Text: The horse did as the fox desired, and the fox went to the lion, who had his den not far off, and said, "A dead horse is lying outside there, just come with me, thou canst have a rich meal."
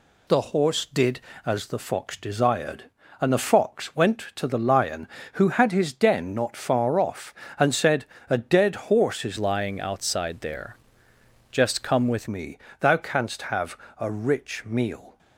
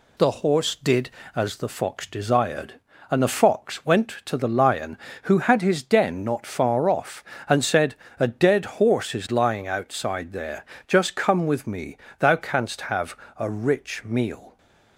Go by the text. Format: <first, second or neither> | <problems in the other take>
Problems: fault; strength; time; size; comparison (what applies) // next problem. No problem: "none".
second | changes voice from "lying" to "with"; from 9.3 to 12.2 s; 2.9 s long // pauses between "have" and "a"; slight; at 13.7 s; 0.22 s long; slight in the second